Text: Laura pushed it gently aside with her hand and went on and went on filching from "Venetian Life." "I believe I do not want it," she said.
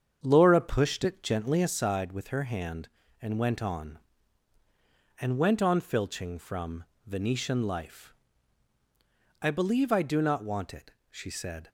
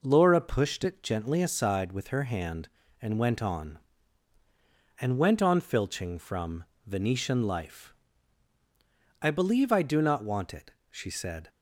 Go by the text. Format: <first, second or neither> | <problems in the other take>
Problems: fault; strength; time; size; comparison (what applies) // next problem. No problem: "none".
second | starts louder than the rest; strong; until 1.8 s; 7.5 dB // pauses between "from" and "Venetian"; slight; at 6.8 s; 0.24 s long; slight in the second